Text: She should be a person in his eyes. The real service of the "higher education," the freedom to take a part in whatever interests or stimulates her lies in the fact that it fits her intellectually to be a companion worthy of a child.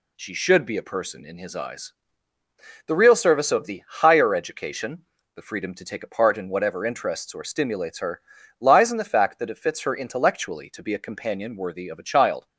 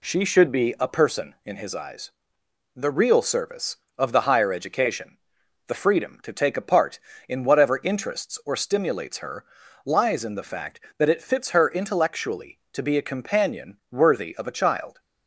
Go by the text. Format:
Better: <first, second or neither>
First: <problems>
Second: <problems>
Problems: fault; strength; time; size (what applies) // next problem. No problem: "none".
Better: neither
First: pauses between "her" and "lies"; slight; at 8.2 s; 0.36 s long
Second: pauses between "her" and "lies"; at 9.4 s; 0.40 s long